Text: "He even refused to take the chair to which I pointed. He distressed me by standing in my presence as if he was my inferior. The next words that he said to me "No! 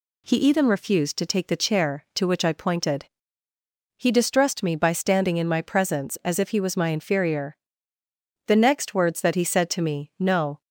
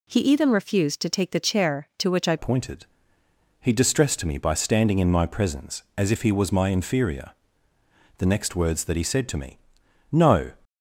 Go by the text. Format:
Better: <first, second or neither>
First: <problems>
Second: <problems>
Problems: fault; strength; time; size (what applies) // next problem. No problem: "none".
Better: first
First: none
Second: changes voice at "pointed"; from 2.3 s on; 8.2 s long // pauses between "me" and "No"; noticeable; at 9.5 s; 0.54 s long